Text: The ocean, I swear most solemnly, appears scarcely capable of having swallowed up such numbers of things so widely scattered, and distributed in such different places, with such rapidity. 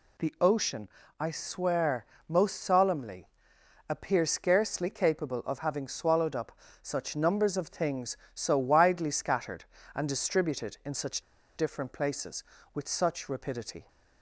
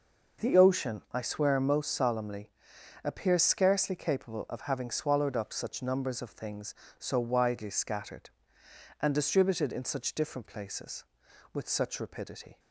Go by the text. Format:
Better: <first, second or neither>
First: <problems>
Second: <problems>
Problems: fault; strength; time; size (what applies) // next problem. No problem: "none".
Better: second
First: pauses between "swear" and "most"; slight; at 2.0 s; 0.22 s long // pauses between "up" and "such"; slight; at 6.5 s; 0.30 s long // pauses between "such" and "different"; slight; at 11.2 s; 0.35 s long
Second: none